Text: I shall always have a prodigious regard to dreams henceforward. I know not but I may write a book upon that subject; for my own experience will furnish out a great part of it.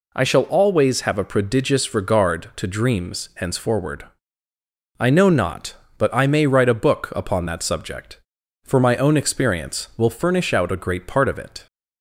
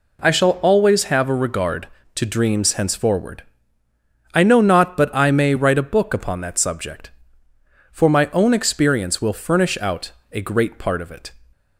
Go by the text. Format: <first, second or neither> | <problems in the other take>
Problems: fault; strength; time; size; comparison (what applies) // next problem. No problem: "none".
first | skips "prodigious"; at 1.3 s // pauses between "out" and "a"; slight; at 10.1 s; 0.22 s long